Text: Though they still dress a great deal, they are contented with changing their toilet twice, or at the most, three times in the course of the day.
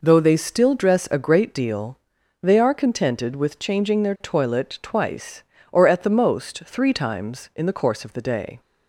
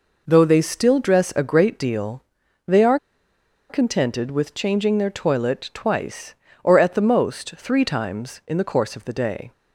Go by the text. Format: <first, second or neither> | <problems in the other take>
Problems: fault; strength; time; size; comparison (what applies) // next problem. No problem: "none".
first | pauses between "are" and "contented"; noticeable; at 2.9 s; 0.72 s long